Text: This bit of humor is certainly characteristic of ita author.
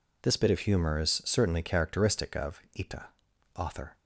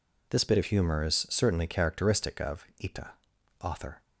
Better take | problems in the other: neither | pauses between "of" and "ita"; slight; the same in both // pauses between "ita" and "author"; noticeable; the same in both

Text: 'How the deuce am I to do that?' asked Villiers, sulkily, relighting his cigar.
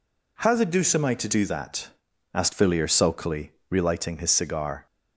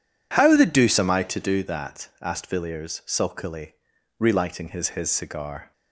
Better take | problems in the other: first | says "his" twice; at 4.9 s

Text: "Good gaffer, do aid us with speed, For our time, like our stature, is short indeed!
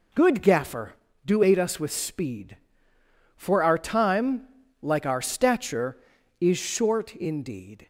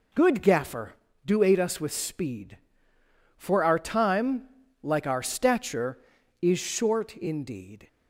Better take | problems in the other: neither | none

